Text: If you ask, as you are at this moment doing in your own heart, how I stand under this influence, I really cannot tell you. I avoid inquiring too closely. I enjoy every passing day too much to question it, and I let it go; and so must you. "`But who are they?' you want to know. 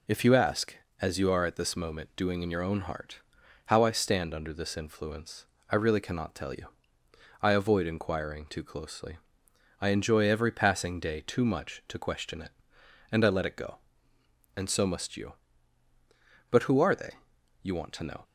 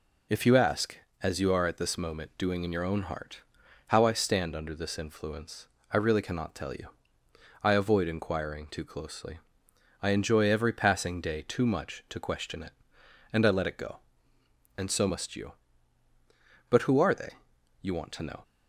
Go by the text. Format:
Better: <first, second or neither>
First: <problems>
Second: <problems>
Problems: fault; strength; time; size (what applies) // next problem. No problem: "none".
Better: neither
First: none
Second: none